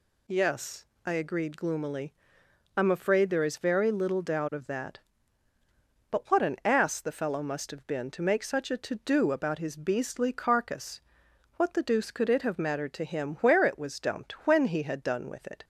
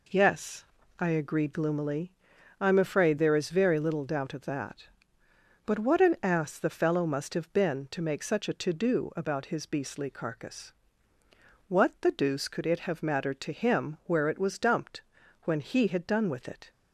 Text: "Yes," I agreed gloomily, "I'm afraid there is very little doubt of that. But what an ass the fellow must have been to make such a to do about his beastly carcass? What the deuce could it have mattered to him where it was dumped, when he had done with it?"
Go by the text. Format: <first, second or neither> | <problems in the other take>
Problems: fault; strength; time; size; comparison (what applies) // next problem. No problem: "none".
neither | none